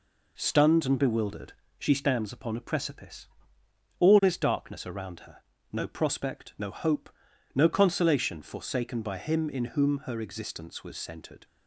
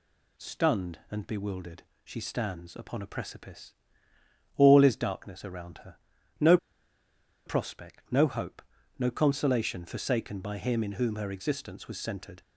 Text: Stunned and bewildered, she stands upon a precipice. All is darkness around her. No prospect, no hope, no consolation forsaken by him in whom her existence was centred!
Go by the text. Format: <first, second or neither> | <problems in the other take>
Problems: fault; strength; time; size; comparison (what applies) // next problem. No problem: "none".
first | pauses between "No" and "prospect"; noticeable; at 6.5 s; 0.89 s long